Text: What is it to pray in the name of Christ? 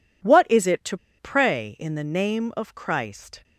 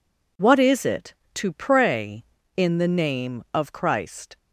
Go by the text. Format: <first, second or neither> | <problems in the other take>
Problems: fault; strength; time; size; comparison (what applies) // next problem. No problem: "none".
second | pauses between "to" and "pray"; slight; at 0.9 s; 0.21 s long